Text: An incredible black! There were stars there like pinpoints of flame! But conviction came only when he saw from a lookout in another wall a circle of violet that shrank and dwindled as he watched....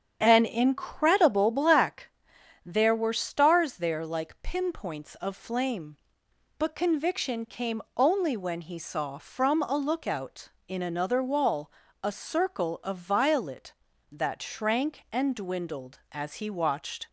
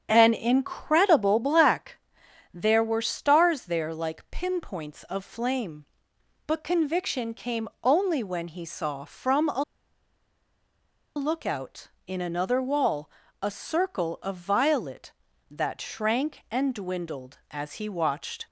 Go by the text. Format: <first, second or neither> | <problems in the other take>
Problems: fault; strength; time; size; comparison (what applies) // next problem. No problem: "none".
first | starts louder than the rest; strong; until 1.1 s; 7.5 dB; strong in the first // pauses between "came" and "only"; slight; at 7.6 s; 0.16 s long; slight in the first // pauses between "a" and "lookout"; strong; at 9.6 s; 1.5 s long // pauses between "wall" and "a"; slight; at 13.0 s; 0.32 s long; slight in the first